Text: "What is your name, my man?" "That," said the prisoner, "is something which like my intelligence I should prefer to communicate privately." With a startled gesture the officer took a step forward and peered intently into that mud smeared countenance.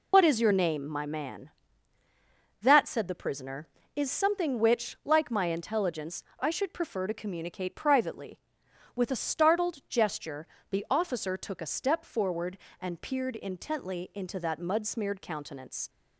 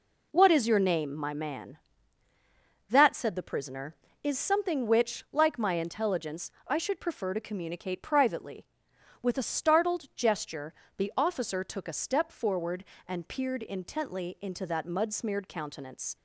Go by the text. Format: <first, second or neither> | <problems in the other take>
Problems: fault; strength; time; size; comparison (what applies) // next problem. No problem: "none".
second | loses the start of "What"; at 0.1 s; 80 ms // pauses between "intelligence" and "I"; slight; at 6.2 s; 0.16 s long; slight in the second // pauses between "gesture" and "the"; slight; at 10.4 s; 0.26 s long; slight in the second